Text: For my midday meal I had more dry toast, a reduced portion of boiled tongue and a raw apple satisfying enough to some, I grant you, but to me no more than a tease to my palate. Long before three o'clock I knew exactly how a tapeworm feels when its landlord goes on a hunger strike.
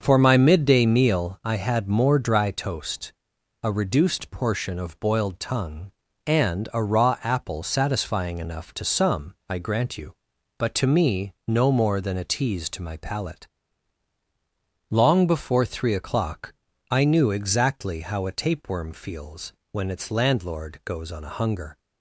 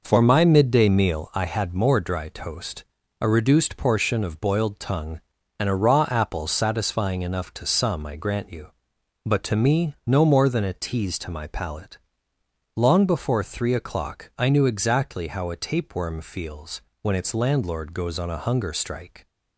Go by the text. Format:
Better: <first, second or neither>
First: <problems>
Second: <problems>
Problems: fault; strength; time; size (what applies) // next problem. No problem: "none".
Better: second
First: starts louder than the rest; until 1.0 s; 6.5 dB // pauses between "o'clock" and "I"; at 16.5 s; 0.38 s long // pauses between "feels" and "when"; slight; at 19.5 s; 0.18 s long // stops before "strike"; at 21.7 s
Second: pauses between "feels" and "when"; slight; at 16.8 s; 0.20 s long